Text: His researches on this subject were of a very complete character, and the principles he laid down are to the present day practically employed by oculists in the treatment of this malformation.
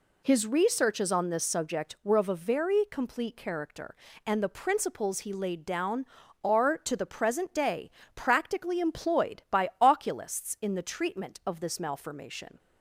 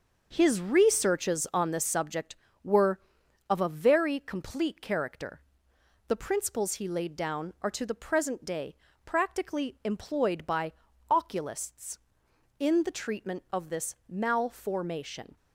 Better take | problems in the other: first | starts louder than the rest; noticeable; until 1.3 s; 6 dB // skips "and"; at 5.7 s // pauses between "day" and "practically"; slight; at 8.7 s; 0.30 s long; slight in the first // pauses between "by" and "oculists"; at 10.7 s; 0.38 s long

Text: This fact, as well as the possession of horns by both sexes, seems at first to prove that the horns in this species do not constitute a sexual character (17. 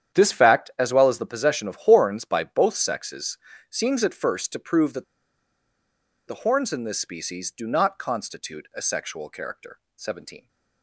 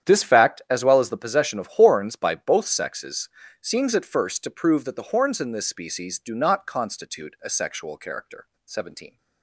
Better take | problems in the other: second | starts louder than the rest; strong; until 1.2 s; 9.5 dB; strong in the second // pauses between "that" and "the"; strong; at 5.0 s; 1.2 s long

